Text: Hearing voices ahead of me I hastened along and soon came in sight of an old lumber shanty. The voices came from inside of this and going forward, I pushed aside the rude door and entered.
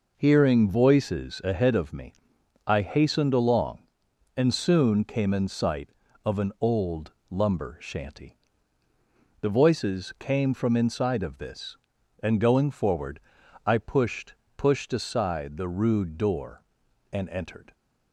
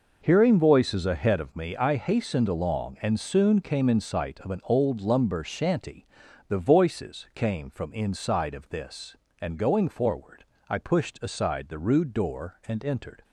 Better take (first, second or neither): second